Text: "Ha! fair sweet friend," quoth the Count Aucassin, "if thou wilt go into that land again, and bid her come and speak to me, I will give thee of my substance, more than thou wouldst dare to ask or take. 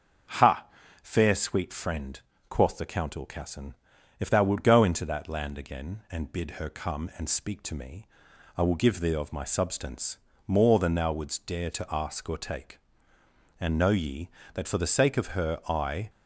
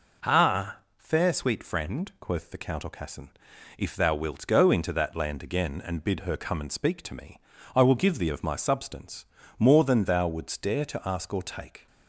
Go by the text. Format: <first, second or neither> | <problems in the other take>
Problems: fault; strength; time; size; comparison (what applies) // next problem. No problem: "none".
second | starts louder than the rest; until 1.7 s; 7 dB // goes on to say "And know ye that for the sake of her I"; strong; from 13.5 s on; 2.5 s long